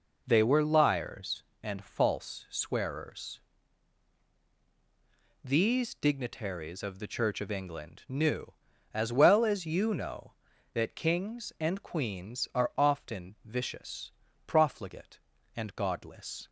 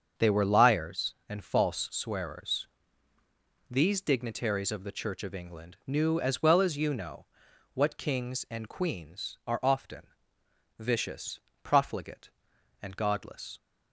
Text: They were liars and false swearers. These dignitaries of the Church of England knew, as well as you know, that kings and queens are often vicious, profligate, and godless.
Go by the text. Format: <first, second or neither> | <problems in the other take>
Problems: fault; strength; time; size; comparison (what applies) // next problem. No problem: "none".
first | starts louder than the rest; until 1.3 s; 7 dB // says "what" for "that"; at 7.7 s // pauses between "often" and "vicious"; noticeable; at 10.0 s; 0.74 s long